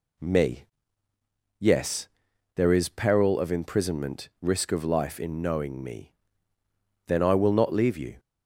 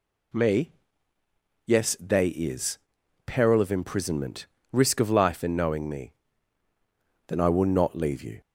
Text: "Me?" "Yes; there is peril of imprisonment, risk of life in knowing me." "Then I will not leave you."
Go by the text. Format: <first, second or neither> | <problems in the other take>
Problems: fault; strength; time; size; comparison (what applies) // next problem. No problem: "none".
first | says "they" for "there"; at 2.0 s // pauses between "is" and "peril"; noticeable; at 2.7 s; 0.48 s long